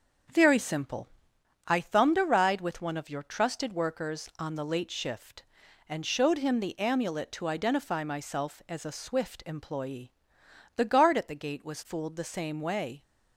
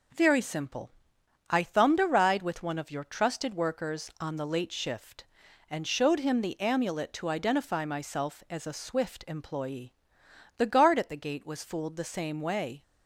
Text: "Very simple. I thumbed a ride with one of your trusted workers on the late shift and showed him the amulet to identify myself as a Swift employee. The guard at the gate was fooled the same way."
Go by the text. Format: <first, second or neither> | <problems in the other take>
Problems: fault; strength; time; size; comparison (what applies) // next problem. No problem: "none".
second | starts louder than the rest; until 1.4 s; 6.5 dB